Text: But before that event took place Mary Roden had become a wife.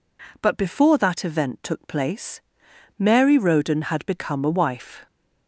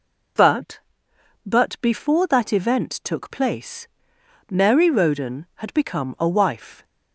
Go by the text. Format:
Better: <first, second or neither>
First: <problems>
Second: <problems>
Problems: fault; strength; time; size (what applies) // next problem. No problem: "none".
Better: first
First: pauses between "place" and "Mary"; noticeable; at 2.4 s; 0.58 s long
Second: says "But" twice; at 1.4 s // pauses between "place" and "Mary"; noticeable; at 3.8 s; 0.64 s long